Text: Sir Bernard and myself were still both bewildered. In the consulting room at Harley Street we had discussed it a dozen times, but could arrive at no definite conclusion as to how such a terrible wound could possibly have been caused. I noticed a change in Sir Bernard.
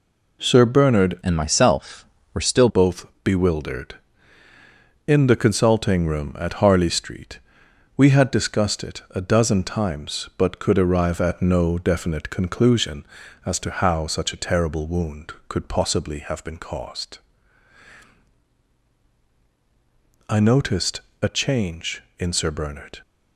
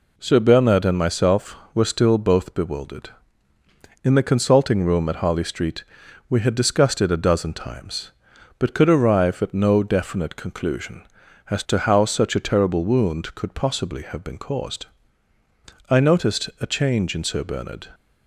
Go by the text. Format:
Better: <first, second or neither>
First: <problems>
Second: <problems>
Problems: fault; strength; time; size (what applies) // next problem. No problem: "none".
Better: second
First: changes voice from "and" to "still"; from 1.2 to 2.6 s; 1.4 s long // pauses between "both" and "bewildered"; slight; at 3.0 s; 0.16 s long // pauses between "Street" and "we"; noticeable; at 7.3 s; 0.58 s long // pauses between "noticed" and "a"; slight; at 21.0 s; 0.20 s long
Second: pauses between "Street" and "we"; noticeable; at 5.8 s; 0.46 s long